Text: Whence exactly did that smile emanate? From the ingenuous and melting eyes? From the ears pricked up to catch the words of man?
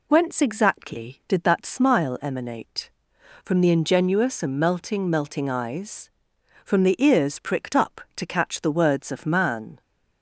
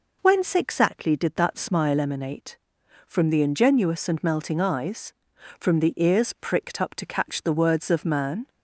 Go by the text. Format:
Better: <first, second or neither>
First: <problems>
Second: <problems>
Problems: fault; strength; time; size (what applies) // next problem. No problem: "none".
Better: second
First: says "melting" twice; at 5.0 s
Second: none